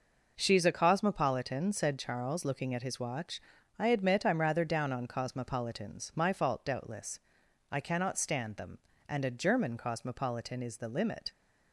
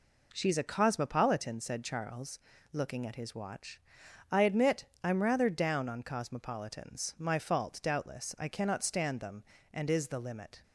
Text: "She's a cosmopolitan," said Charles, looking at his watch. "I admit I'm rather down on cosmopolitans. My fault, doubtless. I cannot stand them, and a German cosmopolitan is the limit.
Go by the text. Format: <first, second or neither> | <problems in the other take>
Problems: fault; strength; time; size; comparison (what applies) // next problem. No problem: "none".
first | pauses between "admit" and "I'm"; slight; at 4.8 s; 0.18 s long // skips "a German cosmopolitan"; at 9.9 s